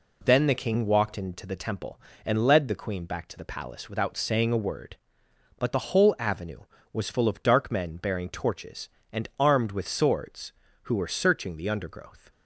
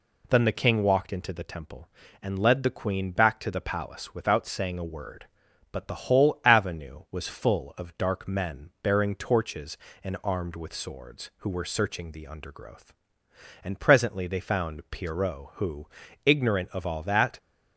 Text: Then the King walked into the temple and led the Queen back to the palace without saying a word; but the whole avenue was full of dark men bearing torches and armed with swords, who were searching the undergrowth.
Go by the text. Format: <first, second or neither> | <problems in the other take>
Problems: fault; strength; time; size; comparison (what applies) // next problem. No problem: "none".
first | goes on to say "And presently they found Pierrot who ignorant of all that"; strong; from 13.6 s on; 3.7 s long